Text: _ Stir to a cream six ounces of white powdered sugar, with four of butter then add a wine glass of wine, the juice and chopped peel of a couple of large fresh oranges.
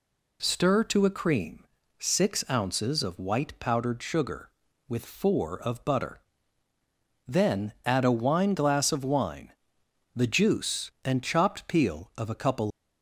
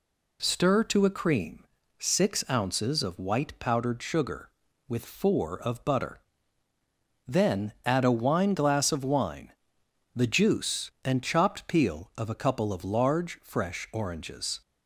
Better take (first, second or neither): second